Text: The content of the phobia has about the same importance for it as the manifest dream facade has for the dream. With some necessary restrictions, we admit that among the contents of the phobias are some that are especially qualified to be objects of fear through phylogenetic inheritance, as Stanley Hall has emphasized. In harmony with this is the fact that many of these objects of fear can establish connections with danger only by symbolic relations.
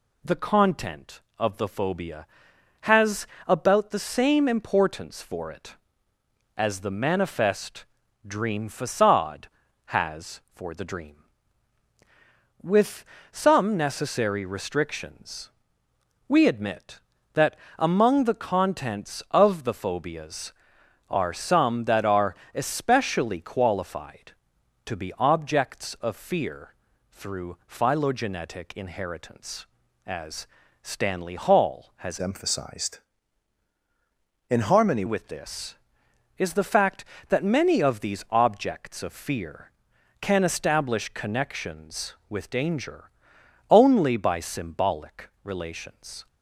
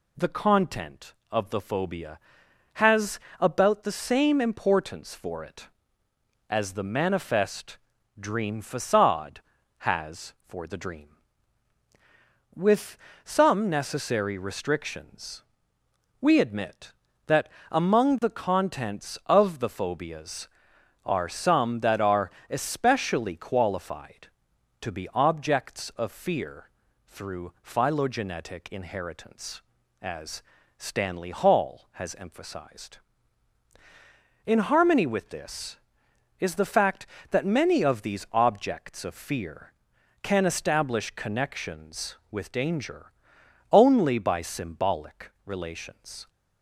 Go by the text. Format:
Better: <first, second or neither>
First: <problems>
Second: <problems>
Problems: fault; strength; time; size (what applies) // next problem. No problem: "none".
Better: second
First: pauses between "has" and "about"; slight; at 3.2 s; 0.18 s long // pauses between "manifest" and "dream"; at 7.8 s; 0.42 s long // pauses between "With" and "some"; slight; at 13.0 s; 0.30 s long // pauses between "that" and "among"; slight; at 17.5 s; 0.20 s long // pauses between "are" and "especially"; slight; at 22.3 s; 0.22 s long // pauses between "fear" and "through"; slight; at 26.7 s; 0.36 s long // pauses between "as" and "Stanley"; slight; at 30.4 s; 0.34 s long // changes voice from "emphasized" to "harmony"; from 32.2 to 35.0 s; 2.8 s long // pauses between "danger" and "only"; noticeable; at 43.0 s; 0.60 s long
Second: pauses between "has" and "about"; slight; at 3.1 s; 0.18 s long // pauses between "manifest" and "dream"; at 7.7 s; 0.42 s long // pauses between "With" and "some"; slight; at 12.9 s; 0.30 s long // pauses between "that" and "among"; slight; at 17.4 s; 0.20 s long // pauses between "are" and "especially"; slight; at 22.2 s; 0.22 s long // pauses between "fear" and "through"; slight; at 26.7 s; 0.36 s long // pauses between "as" and "Stanley"; slight; at 30.4 s; 0.34 s long // pauses between "danger" and "only"; noticeable; at 43.1 s; 0.60 s long